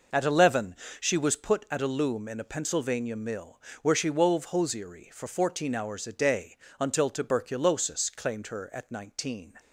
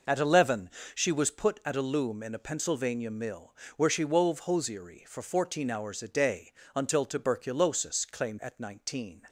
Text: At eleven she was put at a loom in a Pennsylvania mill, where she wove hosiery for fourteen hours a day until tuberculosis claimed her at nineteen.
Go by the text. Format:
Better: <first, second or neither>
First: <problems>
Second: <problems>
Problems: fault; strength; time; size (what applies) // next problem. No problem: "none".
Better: first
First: pauses between "eleven" and "she"; slight; at 0.7 s; 0.24 s long // pauses between "day" and "until"; slight; at 6.5 s; 0.22 s long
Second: pauses between "eleven" and "she"; slight; at 0.7 s; 0.24 s long // pauses between "day" and "until"; slight; at 6.5 s; 0.22 s long // skips "her"; at 8.3 s